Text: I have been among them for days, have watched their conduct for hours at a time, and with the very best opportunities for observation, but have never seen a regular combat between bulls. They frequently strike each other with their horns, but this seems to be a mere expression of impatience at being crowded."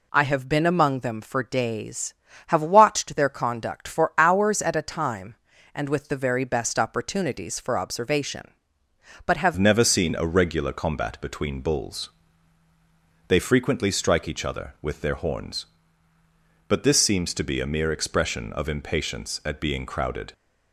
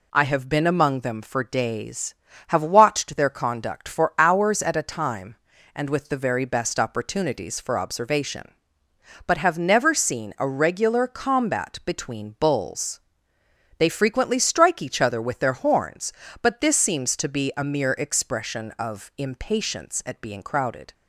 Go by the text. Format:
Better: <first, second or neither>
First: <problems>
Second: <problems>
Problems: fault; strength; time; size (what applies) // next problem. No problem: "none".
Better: second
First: changes voice at "never"; from 9.5 s on; 10.8 s long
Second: none